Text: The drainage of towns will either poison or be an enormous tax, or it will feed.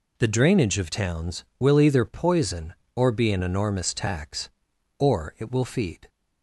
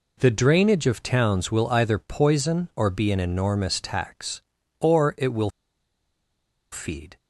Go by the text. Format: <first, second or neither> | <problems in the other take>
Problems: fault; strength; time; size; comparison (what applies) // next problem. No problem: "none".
first | pauses between "will" and "feed"; at 5.5 s; 1.2 s long